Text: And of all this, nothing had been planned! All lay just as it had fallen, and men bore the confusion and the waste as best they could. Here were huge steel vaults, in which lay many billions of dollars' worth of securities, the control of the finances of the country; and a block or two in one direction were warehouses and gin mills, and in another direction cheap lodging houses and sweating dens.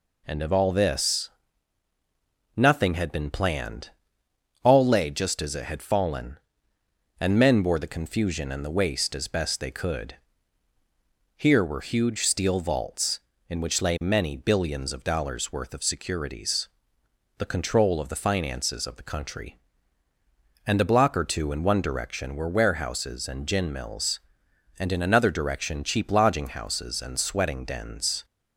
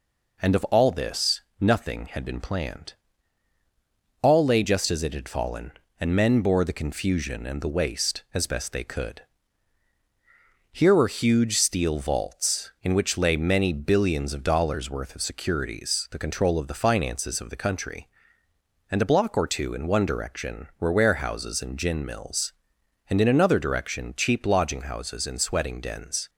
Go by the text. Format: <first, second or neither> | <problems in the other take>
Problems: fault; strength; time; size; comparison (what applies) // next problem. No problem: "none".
neither | none